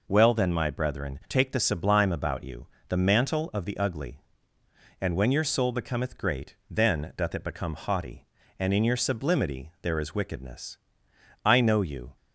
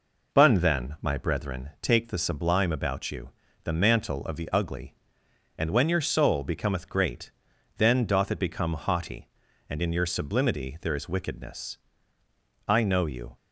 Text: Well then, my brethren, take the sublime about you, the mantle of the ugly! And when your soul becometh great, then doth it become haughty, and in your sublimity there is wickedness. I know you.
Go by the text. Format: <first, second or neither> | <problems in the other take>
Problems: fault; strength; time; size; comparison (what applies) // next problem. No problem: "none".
first | says "Bun" for "Well"; at 0.3 s